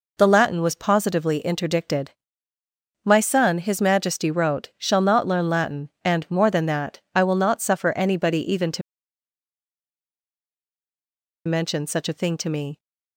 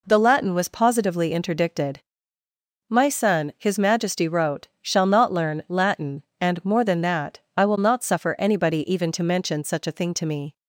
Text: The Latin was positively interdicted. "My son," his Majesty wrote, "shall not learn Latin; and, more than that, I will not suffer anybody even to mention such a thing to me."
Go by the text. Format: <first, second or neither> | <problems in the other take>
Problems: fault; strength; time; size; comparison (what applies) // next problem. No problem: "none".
second | pauses between "to" and "mention"; strong; at 8.8 s; 2.6 s long